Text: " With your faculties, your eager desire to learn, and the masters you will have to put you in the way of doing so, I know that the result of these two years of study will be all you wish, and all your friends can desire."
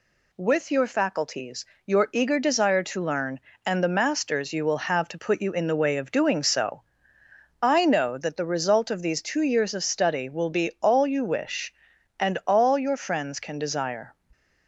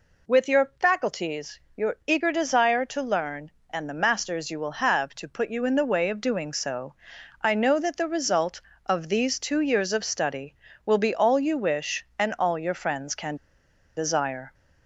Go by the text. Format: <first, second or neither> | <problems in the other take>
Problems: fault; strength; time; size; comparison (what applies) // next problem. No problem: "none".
first | pauses between "can" and "desire"; noticeable; at 13.3 s; 0.60 s long